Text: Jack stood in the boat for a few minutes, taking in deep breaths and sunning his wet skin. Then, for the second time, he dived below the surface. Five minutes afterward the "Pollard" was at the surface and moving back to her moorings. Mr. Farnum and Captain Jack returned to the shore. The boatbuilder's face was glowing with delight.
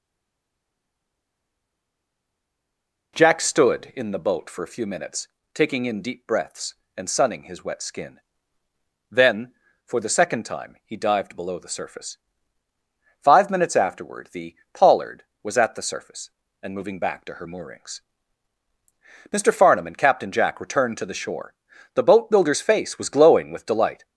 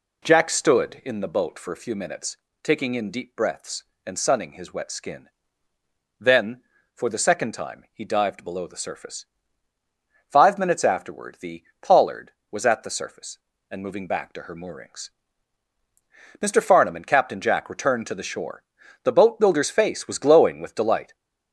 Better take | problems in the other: second | stays silent before the first word; strong; until 3.1 s; 3.1 s long // pauses between "the" and "Pollard"; slight; at 14.5 s; 0.16 s long; slight in the second

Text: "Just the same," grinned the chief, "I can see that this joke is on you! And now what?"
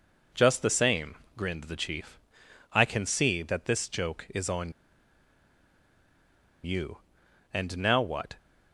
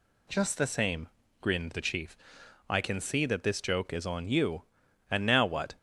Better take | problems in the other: second | pauses between "on" and "you"; strong; at 4.7 s; 1.9 s long

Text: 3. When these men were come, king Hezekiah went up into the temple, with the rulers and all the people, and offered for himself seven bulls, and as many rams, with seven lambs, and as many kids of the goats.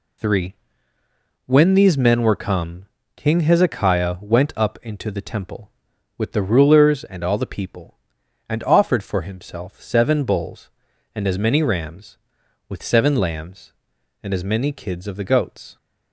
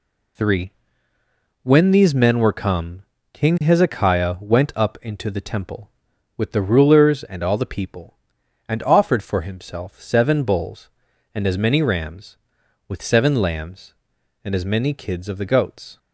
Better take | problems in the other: neither | none

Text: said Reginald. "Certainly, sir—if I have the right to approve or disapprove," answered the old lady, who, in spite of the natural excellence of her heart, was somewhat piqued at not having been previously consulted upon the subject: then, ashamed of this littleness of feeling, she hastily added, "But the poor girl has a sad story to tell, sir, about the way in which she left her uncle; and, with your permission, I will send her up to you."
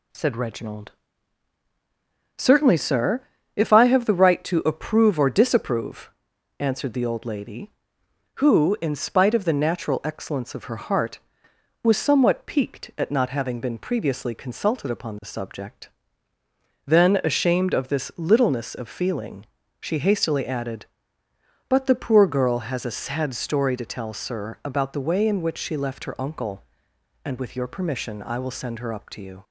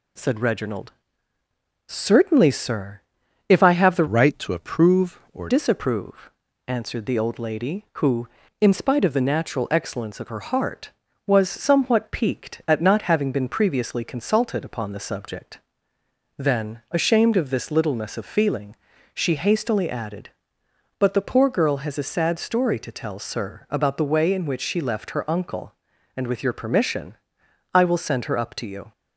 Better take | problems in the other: first | changes voice from "right" to "or"; from 4.0 to 5.4 s; 1.4 s long

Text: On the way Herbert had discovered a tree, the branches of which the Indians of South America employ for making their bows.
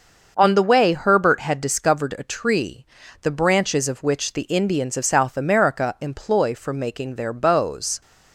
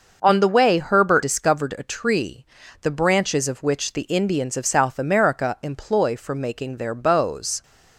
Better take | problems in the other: first | starts louder than the rest; noticeable; until 1.2 s; 6 dB; also in the first // skips "had"; at 1.2 s

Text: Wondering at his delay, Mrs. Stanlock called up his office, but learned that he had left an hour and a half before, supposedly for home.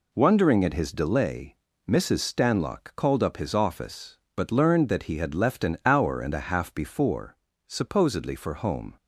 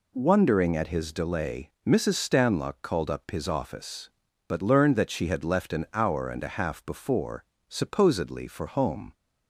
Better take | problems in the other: first | says "she" for "he"; at 5.1 s

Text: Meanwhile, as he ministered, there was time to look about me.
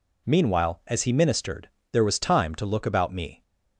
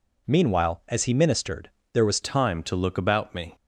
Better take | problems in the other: first | changes voice at "time"; from 2.2 s on; 1.3 s long

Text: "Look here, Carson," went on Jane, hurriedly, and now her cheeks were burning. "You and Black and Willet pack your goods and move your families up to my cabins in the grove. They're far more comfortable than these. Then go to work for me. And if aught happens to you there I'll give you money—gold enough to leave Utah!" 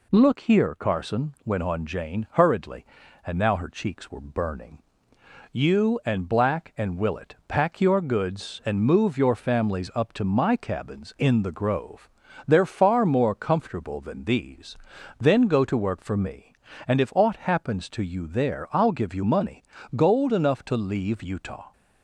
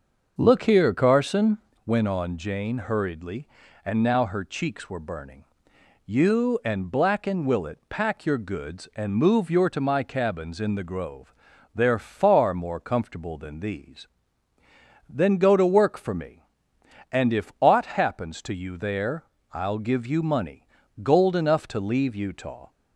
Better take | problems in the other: first | starts louder than the rest; until 1.4 s; 6.5 dB // skips "families up"; at 9.6 s // pauses between "there" and "I'll"; slight; at 19.2 s; 0.30 s long

